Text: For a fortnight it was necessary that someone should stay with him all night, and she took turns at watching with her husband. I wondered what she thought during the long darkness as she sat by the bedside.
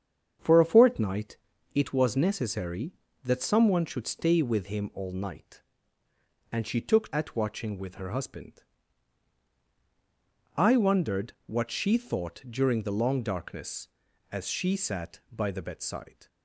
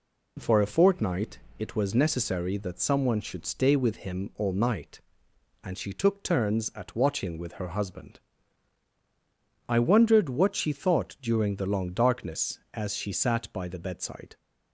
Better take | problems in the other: second | starts louder than the rest; strong; until 1.7 s; 7.5 dB // pauses between "fortnight" and "it"; at 1.3 s; 0.38 s long; slight in the second // skips "turns"; at 7.1 s

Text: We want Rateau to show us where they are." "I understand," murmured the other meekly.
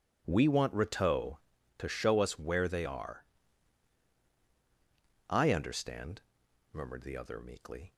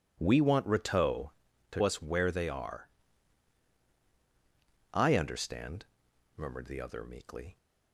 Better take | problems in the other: first | skips "show"; at 1.8 s

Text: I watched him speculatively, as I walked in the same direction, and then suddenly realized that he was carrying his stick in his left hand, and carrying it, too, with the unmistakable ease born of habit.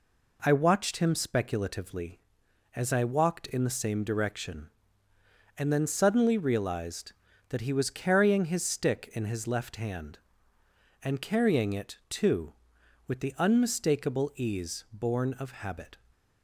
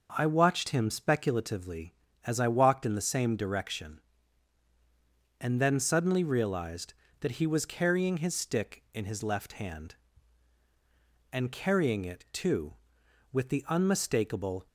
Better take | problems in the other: first | starts louder than the rest; noticeable; until 1.1 s; 6 dB // stops before "ease born of habit"; at 14.6 s

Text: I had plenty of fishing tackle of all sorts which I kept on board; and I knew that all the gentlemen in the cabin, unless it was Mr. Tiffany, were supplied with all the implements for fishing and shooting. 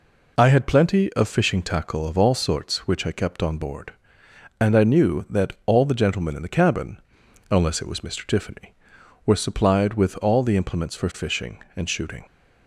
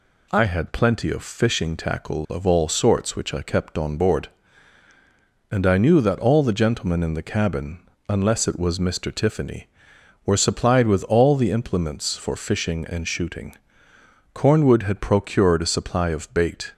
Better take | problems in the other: first | goes on to say "Cornwood had procured a supply of bait"; strong; from 14.3 s on; 2.4 s long

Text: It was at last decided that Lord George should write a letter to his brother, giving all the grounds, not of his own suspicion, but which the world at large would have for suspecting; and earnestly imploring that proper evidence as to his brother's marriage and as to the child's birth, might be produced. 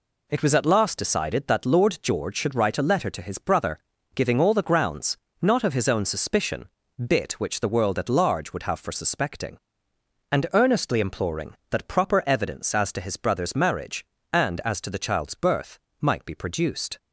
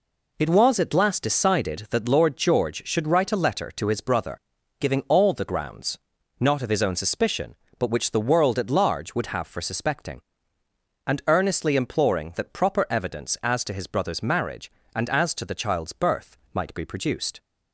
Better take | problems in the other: second | says "bit" for "but"; at 7.0 s

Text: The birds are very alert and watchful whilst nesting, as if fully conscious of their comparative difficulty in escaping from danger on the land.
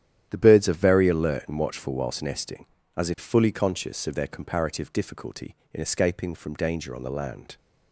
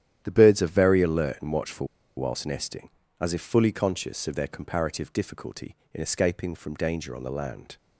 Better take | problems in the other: first | starts louder than the rest; strong; until 1.2 s; 11 dB; strong in the first // pauses between "watchful" and "whilst"; slight; at 1.8 s; 0.30 s long

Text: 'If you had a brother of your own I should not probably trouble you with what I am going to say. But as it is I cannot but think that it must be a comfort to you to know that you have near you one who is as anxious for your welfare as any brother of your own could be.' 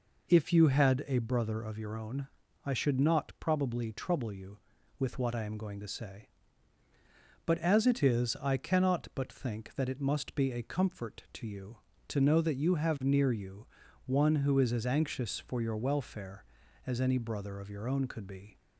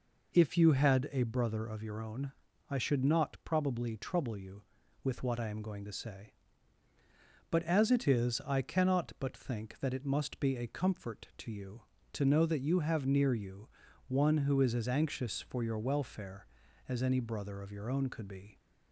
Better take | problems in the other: neither | pauses between "own" and "I"; slight; the same in both // pauses between "you" and "one"; the same in both

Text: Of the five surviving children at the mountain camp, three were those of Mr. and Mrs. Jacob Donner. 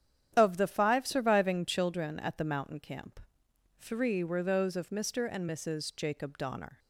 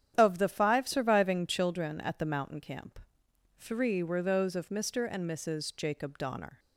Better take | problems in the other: neither | starts louder than the rest; strong; the same in both

